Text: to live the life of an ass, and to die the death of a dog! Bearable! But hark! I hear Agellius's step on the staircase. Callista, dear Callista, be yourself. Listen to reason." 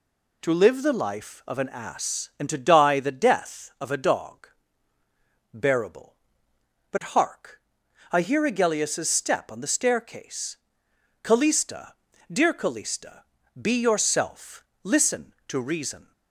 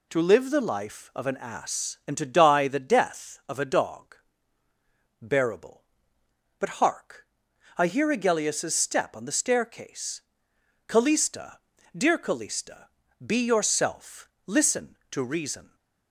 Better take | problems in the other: neither | none

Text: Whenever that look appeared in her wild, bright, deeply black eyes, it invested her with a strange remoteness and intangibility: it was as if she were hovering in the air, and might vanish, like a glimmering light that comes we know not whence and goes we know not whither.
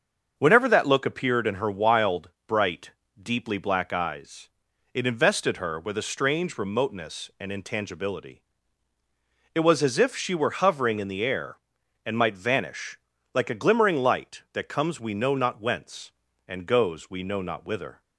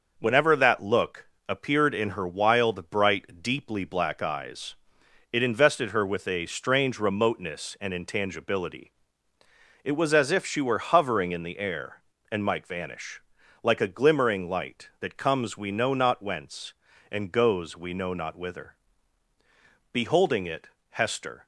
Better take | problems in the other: first | starts louder than the rest; until 1.1 s; 6 dB; also in the first // pauses between "look" and "appeared"; slight; at 1.2 s; 0.20 s long // goes on to say "Beholding it Hester"; from 19.9 s on; 1.5 s long

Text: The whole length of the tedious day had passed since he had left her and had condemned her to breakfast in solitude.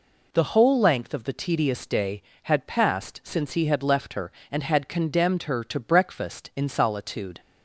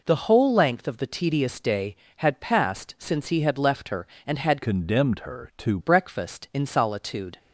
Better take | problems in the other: first | changes voice from "condemned" to "to"; from 4.6 to 5.7 s; 1.1 s long

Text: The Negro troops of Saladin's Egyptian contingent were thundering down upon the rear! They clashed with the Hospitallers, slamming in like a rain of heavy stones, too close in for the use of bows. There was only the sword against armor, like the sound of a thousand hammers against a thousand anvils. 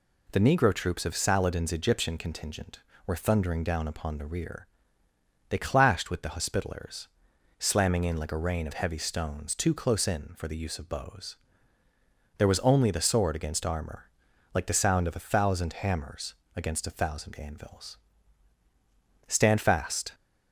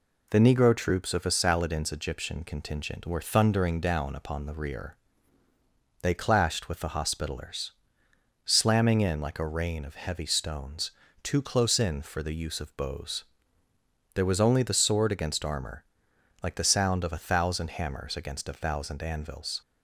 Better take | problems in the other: second | pauses between "hammers" and "against"; slight; at 16.3 s; 0.22 s long // goes on to say "Stand fast"; noticeable; from 19.2 s on; 0.86 s long

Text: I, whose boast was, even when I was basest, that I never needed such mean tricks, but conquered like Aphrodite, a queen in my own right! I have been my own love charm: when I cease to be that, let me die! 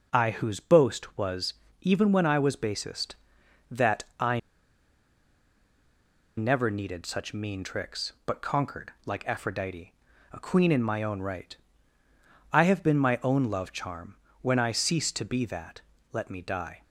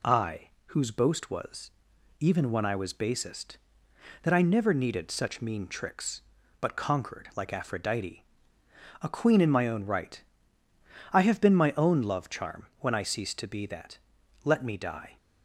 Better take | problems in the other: second | pauses between "I" and "never"; strong; at 4.3 s; 1.9 s long // pauses between "conquered" and "like"; slight; at 8.9 s; 0.16 s long

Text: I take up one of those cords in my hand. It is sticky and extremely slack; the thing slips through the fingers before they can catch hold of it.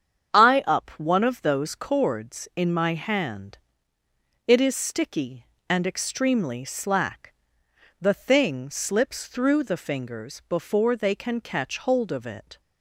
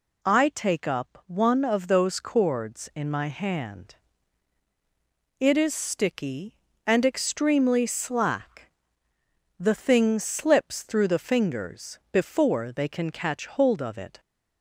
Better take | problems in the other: second | starts louder than the rest; strong; until 1.4 s; 8 dB // skips "take"; at 0.6 s

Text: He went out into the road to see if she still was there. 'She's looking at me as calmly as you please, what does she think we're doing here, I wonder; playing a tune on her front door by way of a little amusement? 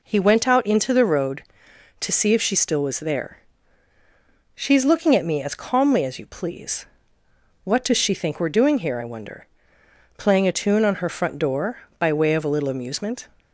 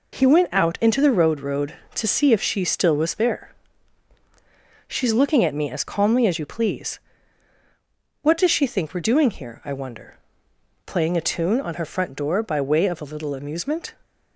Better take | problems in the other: first | says "road" twice; at 1.3 s

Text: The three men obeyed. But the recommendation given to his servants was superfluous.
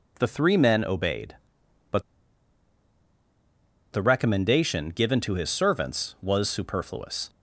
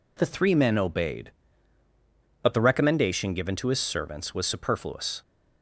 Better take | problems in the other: second | pauses between "But" and "the"; strong; at 2.0 s; 1.9 s long

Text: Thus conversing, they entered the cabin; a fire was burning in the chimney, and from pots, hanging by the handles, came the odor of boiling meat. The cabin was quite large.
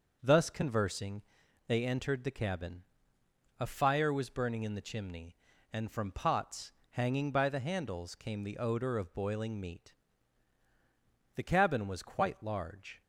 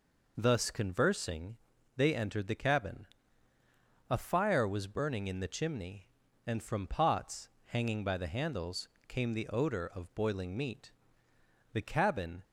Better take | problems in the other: first | stops before "was quite large"; at 12.4 s

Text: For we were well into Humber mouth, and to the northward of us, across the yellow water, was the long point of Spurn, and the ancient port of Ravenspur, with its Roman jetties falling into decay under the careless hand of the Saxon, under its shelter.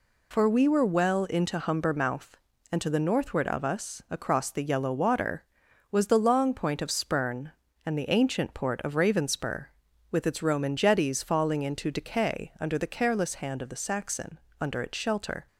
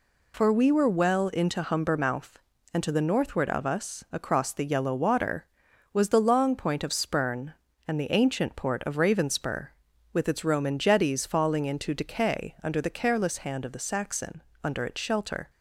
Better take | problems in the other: neither | none

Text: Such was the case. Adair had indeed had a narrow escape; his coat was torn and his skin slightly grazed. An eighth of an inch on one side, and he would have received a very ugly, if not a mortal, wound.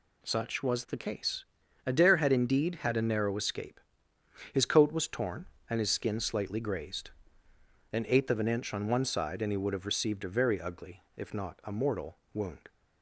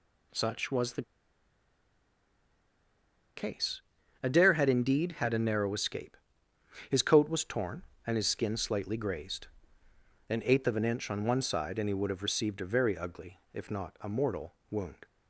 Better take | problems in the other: first | pauses between "the" and "case"; strong; at 1.0 s; 2.3 s long

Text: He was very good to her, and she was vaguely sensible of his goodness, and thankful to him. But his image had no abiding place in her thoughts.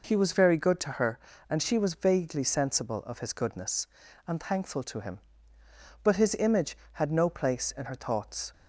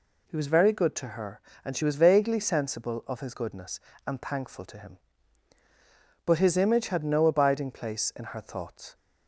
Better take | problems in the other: second | skips "abiding"; at 7.2 s

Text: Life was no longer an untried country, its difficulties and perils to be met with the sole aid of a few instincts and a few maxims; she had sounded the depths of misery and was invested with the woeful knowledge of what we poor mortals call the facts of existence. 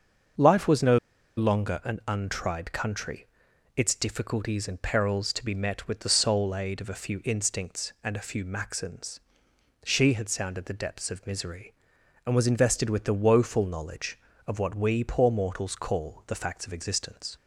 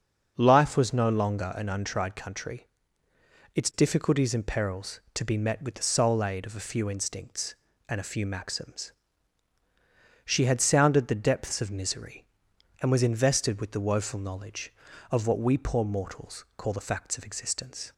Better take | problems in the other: second | starts louder than the rest; until 1.7 s; 6.5 dB; also in the second // pauses between "no" and "longer"; at 0.9 s; 0.39 s long

